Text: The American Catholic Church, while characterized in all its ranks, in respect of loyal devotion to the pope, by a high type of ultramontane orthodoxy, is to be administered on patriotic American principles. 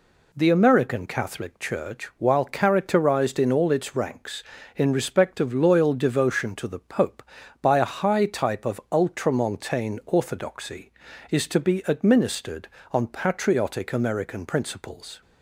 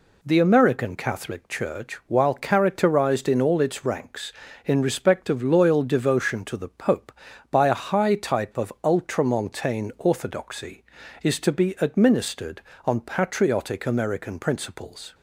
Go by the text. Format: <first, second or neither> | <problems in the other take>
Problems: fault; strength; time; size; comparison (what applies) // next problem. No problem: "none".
neither | none